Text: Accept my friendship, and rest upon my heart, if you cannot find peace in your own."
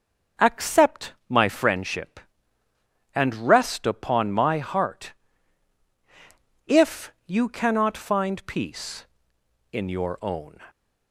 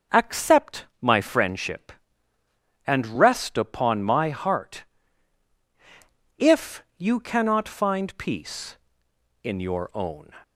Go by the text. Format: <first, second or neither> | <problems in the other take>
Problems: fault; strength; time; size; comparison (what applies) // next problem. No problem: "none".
neither | starts louder than the rest; the same in both // pauses between "Accept" and "my"; slight; the same in both